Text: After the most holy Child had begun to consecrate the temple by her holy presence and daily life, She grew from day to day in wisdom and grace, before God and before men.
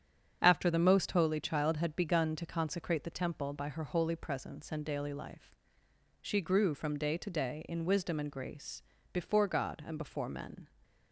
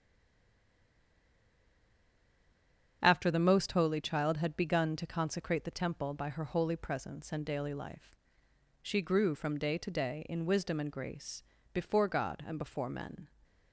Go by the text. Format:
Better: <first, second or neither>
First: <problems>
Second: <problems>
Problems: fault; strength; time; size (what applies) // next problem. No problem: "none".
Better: first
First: starts louder than the rest; strong; until 1.4 s; 8 dB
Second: stays silent before the first word; strong; until 3.0 s; 3.0 s long // starts louder than the rest; strong; until 4.0 s; 8 dB